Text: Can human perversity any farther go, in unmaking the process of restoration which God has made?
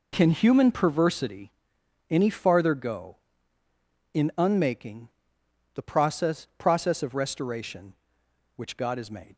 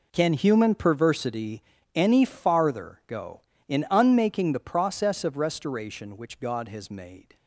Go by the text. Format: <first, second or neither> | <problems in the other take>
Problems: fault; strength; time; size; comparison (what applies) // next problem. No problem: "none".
second | pauses between "perversity" and "any"; noticeable; at 1.4 s; 0.58 s long; slight in the second // pauses between "unmaking" and "the"; noticeable; at 5.0 s; 0.66 s long // says "process" twice; at 6.5 s